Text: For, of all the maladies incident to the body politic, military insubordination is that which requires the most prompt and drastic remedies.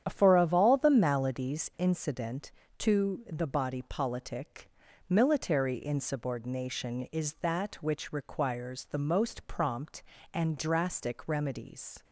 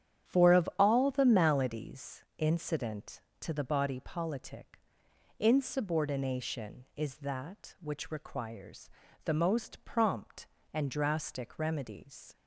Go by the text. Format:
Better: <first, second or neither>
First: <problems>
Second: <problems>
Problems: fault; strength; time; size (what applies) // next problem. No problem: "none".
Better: first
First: starts louder than the rest; strong; until 1.0 s; 9.5 dB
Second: starts louder than the rest; strong; until 1.3 s; 9.5 dB // pauses between "maladies" and "incident"; slight; at 2.2 s; 0.16 s long // skips "military"; at 5.0 s // pauses between "requires" and "the"; slight; at 8.8 s; 0.36 s long